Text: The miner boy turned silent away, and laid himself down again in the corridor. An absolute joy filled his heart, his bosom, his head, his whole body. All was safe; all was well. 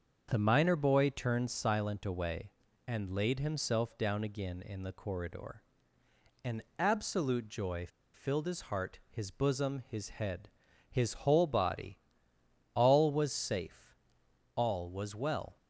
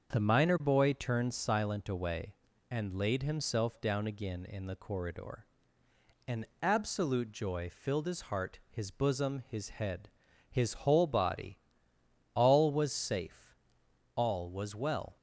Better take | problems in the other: second | starts louder than the rest; until 1.3 s; 6.5 dB; also in the second // pauses between "An" and "absolute"; slight; at 6.6 s; 0.16 s long; slight in the second // pauses between "joy" and "filled"; slight; at 7.8 s; 0.26 s long

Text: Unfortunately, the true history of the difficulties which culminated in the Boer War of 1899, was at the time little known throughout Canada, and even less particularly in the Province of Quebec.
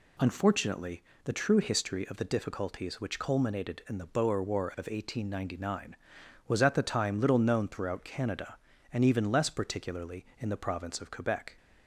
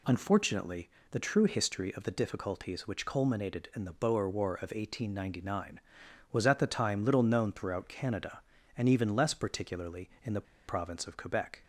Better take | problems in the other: first | pauses between "the" and "Province"; slight; at 10.4 s; 0.24 s long

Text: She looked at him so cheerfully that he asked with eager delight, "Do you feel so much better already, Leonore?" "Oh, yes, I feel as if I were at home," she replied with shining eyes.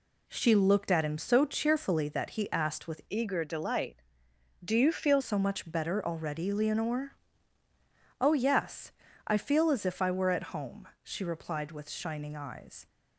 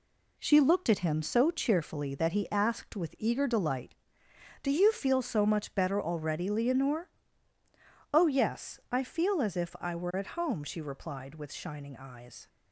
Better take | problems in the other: second | changes voice from "eager" to "feel"; from 3.1 to 5.2 s; 2.1 s long

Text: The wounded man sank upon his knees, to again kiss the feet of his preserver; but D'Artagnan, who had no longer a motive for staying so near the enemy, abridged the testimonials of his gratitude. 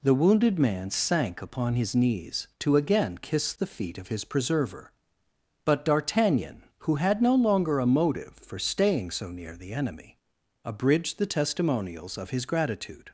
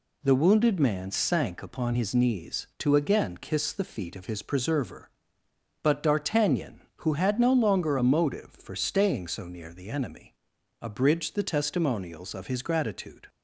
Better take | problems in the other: neither | none

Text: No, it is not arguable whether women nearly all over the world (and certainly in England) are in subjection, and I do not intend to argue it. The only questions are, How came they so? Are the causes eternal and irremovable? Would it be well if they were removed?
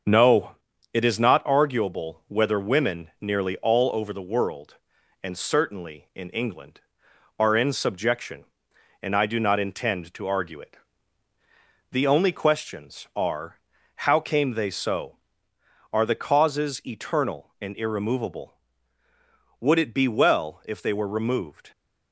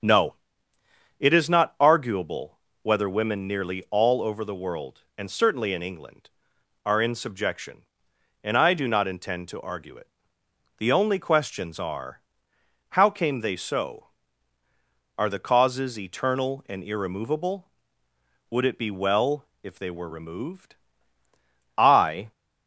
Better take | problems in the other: first | starts louder than the rest; strong; until 1.9 s; 7.5 dB; also in the first // pauses between "arguable" and "whether"; slight; at 2.5 s; 0.24 s long // pauses between "well" and "if"; slight; at 19.4 s; 0.16 s long // goes on to say "I"; from 21.7 s on; 0.54 s long

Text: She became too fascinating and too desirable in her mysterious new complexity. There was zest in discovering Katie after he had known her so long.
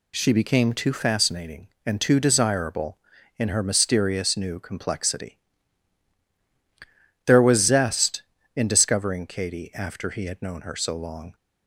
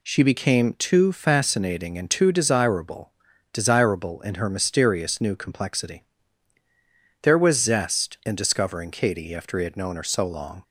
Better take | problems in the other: first | says "desirable" twice; at 3.5 s

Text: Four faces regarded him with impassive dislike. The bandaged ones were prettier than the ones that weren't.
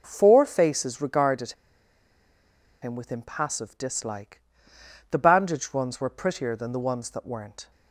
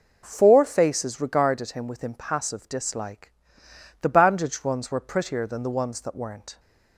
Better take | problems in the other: second | pauses between "regarded" and "him"; strong; at 1.5 s; 1.2 s long

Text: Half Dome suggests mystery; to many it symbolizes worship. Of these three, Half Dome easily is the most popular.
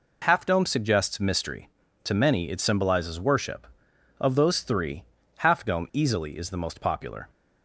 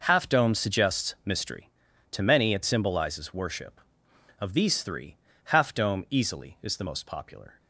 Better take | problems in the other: second | says "those" for "these"; at 4.3 s

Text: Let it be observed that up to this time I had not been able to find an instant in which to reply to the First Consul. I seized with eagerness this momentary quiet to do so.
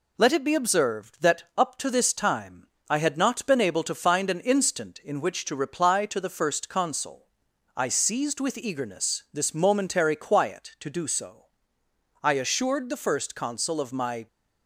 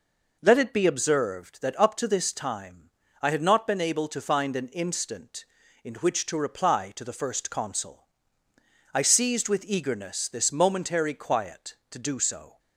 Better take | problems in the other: second | pauses between "time" and "I"; slight; at 2.6 s; 0.22 s long; slight in the second // goes on to say "I assured the First Consul of my"; strong; from 12.2 s on; 2.0 s long

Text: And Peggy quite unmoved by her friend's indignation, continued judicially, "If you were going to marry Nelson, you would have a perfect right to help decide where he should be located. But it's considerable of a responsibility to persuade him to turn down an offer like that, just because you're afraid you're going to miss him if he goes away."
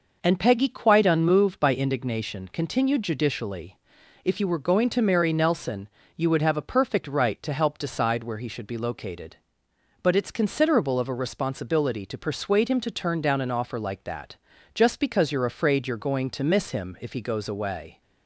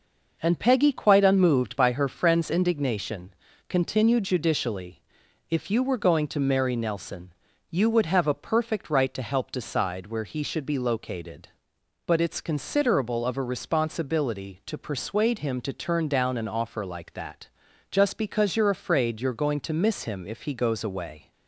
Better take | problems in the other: second | skips "her friend's"; at 1.7 s

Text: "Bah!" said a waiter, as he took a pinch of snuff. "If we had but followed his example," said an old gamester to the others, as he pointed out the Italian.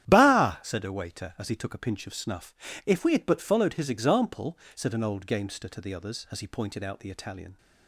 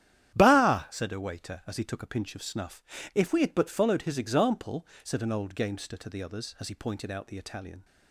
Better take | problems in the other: neither | starts louder than the rest; strong; the same in both

